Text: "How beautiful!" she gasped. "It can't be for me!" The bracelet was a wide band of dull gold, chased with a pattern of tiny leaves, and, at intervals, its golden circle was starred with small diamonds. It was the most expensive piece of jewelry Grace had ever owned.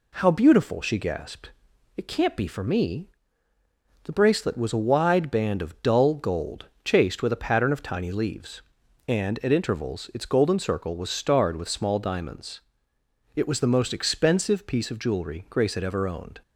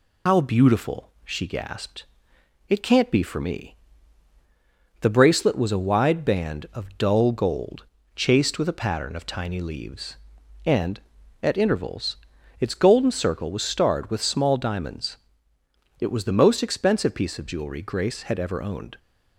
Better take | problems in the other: first | loses the start of "How"; at 0.2 s; 130 ms

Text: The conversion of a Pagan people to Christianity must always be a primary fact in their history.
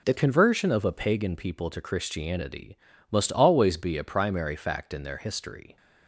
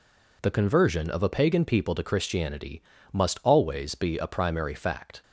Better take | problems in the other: first | pauses between "Christianity" and "must"; slight; at 2.8 s; 0.32 s long; slight in the first // stops before "in their history"; at 5.2 s

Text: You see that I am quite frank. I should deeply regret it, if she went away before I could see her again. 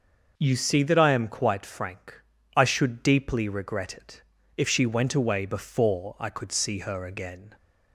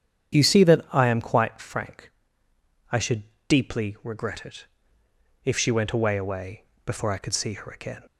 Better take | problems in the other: first | starts louder than the rest; strong; until 1.4 s; 8.5 dB // pauses between "should" and "deeply"; slight; at 3.2 s; 0.26 s long // says "away" twice; at 6.1 s

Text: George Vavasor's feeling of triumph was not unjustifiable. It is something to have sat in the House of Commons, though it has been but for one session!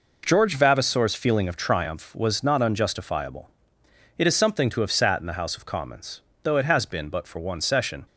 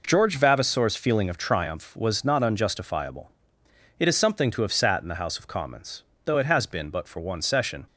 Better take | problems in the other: neither | none

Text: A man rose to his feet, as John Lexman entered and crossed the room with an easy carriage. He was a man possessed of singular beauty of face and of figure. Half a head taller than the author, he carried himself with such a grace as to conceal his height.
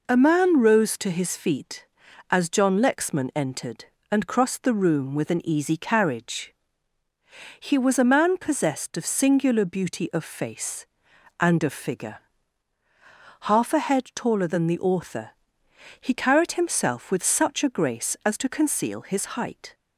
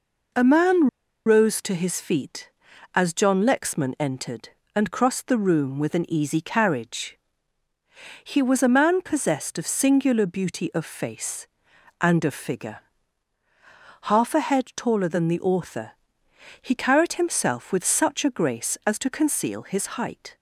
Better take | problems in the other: first | pauses between "man" and "rose"; at 0.8 s; 0.40 s long

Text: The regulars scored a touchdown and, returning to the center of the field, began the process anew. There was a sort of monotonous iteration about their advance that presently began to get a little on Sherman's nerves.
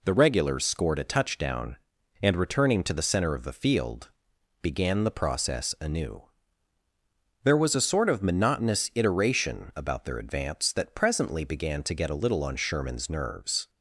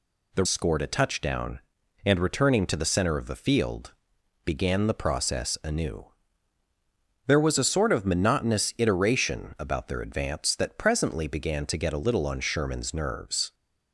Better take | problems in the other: first | skips "regulars"; at 0.4 s

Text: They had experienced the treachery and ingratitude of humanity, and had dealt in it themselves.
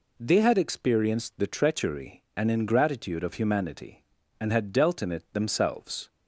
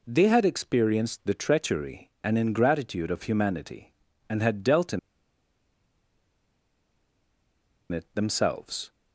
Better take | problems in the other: first | pauses between "in" and "it"; strong; at 4.9 s; 2.9 s long

